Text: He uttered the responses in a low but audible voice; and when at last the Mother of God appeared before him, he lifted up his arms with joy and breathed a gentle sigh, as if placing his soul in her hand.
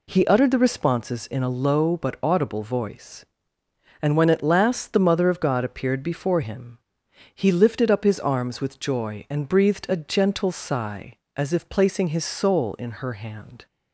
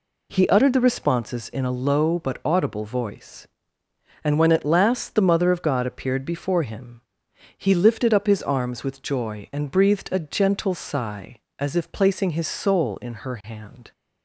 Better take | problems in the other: neither | none

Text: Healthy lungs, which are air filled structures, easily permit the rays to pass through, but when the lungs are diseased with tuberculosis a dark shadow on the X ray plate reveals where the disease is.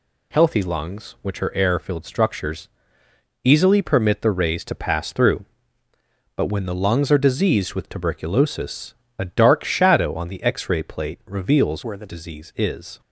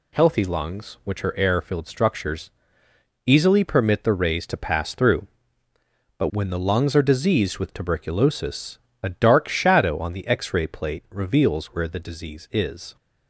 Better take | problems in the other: second | pauses between "tuberculosis" and "a"; slight; at 8.9 s; 0.24 s long; slight in the second // changes voice from "where" to "the"; from 11.8 to 12.0 s; 0.2 s long

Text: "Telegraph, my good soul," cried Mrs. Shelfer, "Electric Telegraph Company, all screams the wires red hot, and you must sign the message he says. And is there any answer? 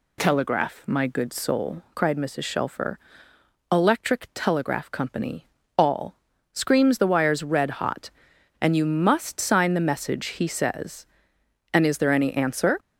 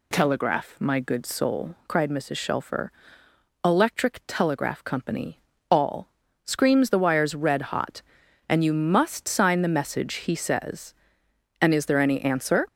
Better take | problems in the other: neither | pauses between "all" and "screams"; slight; the same in both

